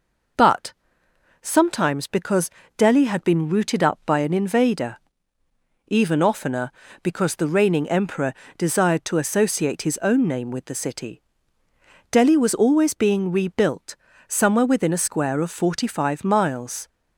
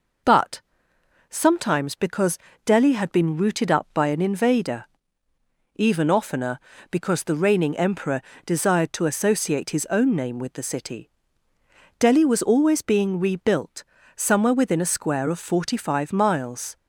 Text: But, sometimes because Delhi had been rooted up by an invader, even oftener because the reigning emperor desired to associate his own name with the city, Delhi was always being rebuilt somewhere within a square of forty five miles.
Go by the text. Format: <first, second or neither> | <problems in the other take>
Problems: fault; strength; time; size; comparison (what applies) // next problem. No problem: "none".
neither | pauses between "because" and "Delhi"; slight; the same in both // pauses between "emperor" and "desired"; slight; the same in both // pauses between "rebuilt" and "somewhere"; slight; the same in both